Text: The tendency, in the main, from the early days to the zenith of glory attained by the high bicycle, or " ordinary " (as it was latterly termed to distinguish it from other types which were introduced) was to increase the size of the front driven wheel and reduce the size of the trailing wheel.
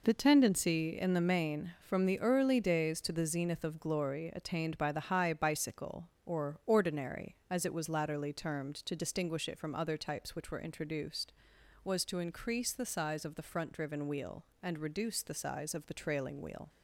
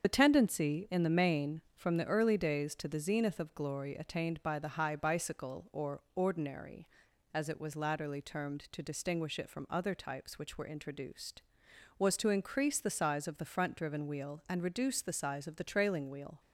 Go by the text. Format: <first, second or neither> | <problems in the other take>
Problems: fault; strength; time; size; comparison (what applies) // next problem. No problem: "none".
first | loses the start of "The"; at 0.0 s; 30 ms // starts louder than the rest; strong; until 1.0 s; 7.5 dB